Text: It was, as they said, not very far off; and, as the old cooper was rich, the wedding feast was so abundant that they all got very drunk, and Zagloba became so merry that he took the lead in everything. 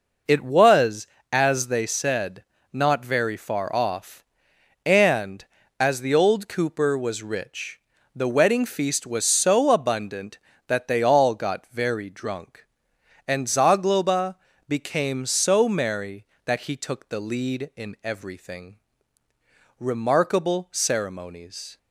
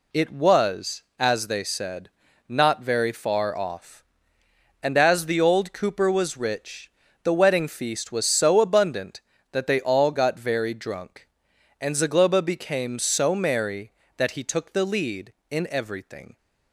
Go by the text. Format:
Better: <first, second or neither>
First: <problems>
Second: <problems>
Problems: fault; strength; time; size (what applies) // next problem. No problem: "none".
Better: second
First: pauses between "Zagloba" and "became"; slight; at 14.3 s; 0.34 s long // goes on to say "Remarkable ceremonies"; strong; from 19.7 s on; 2.0 s long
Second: none